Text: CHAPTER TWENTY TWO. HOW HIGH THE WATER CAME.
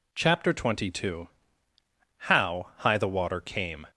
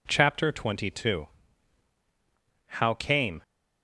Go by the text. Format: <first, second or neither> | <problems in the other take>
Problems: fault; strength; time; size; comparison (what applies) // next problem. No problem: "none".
first | skips "HIGH THE WATER"; at 2.9 s